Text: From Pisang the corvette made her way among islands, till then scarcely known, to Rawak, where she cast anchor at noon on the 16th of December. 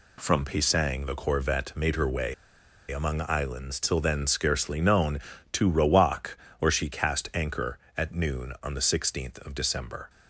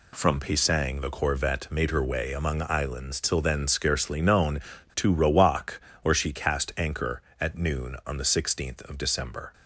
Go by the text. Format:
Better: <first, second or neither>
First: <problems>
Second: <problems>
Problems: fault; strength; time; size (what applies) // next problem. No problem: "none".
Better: second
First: pauses between "way" and "among"; noticeable; at 2.3 s; 0.57 s long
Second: none